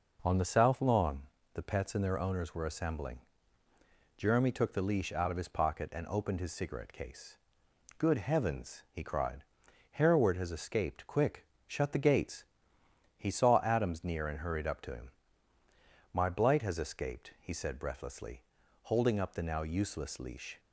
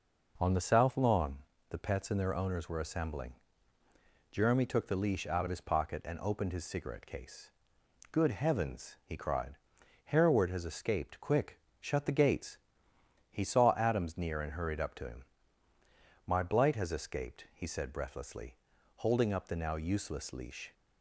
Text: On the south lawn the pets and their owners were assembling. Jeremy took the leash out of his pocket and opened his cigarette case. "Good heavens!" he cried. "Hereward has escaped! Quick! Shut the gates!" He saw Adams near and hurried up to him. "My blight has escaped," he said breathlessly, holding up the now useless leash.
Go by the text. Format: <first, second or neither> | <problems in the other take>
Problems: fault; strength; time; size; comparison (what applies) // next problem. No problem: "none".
neither | pauses between "lawn" and "the"; slight; the same in both